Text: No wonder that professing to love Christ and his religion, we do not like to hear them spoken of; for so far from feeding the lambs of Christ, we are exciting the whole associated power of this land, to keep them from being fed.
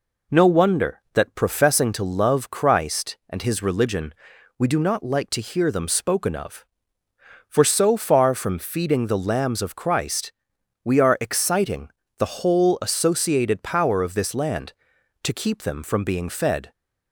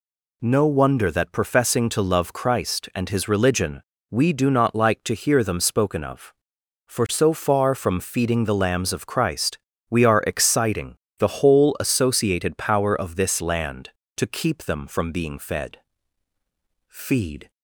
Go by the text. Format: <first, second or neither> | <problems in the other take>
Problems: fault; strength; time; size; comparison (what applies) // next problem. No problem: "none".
first | pauses between "exciting" and "the"; slight; at 10.9 s; 0.22 s long; slight in the first // goes on to say "Feed"; noticeable; from 16.8 s on; 0.62 s long